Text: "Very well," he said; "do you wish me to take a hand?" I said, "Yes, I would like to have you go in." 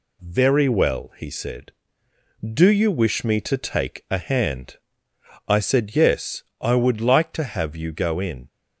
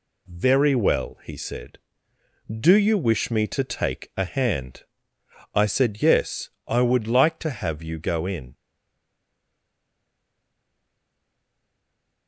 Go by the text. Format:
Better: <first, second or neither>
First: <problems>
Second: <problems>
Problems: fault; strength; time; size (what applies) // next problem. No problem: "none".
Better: first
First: none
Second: stays silent after the last word; strong; from 8.5 s on; 3.7 s long